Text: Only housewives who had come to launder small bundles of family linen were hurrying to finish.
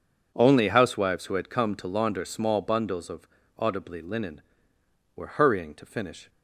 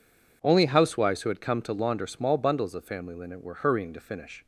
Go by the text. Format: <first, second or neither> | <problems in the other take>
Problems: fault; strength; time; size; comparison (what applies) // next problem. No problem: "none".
second | says "audibly" for "family"; at 3.5 s